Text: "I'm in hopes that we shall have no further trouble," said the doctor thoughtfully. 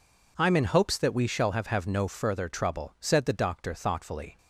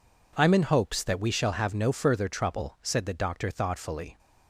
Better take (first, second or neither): second